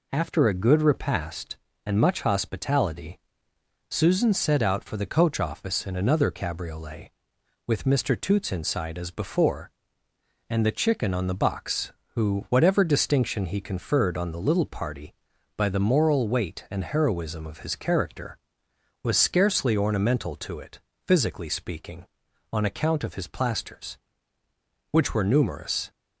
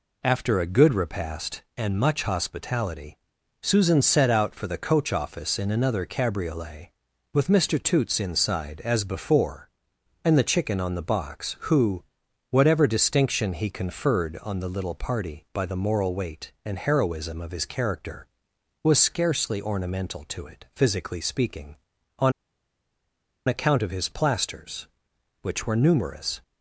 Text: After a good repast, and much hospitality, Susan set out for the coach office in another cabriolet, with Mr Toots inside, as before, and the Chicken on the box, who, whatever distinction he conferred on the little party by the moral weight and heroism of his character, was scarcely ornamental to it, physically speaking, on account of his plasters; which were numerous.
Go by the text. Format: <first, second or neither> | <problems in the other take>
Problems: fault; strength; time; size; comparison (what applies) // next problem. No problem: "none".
first | pauses between "on" and "account"; at 22.3 s; 1.1 s long